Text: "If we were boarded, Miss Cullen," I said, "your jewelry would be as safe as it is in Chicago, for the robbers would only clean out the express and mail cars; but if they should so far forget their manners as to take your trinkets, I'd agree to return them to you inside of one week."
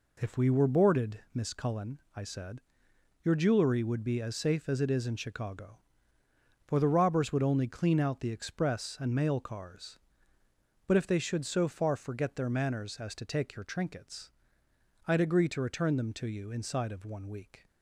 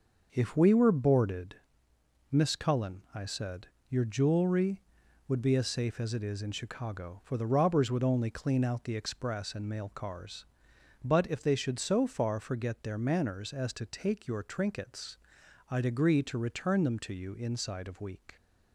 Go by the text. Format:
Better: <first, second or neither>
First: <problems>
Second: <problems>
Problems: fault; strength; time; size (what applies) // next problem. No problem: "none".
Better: first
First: none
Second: starts louder than the rest; noticeable; until 1.3 s; 6 dB // skips "one"; at 17.9 s